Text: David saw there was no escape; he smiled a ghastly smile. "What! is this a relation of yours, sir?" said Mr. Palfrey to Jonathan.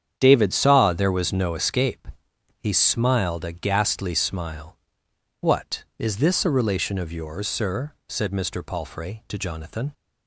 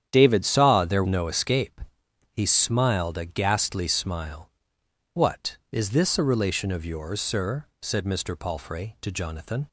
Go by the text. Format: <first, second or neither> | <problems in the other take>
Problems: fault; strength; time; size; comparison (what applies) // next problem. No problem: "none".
first | starts louder than the rest; strong; until 1.1 s; 9.5 dB; strong in the first // skips "was"; at 1.0 s